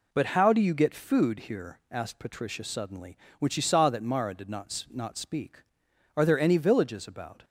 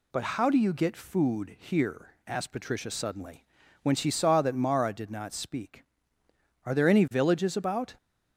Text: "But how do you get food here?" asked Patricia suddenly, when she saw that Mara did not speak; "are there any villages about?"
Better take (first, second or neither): second